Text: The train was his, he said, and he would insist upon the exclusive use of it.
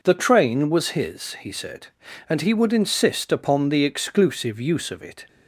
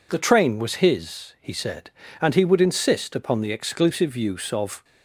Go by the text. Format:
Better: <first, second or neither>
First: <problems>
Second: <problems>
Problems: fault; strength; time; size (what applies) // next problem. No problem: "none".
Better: first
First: none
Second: stops before "it"; at 4.8 s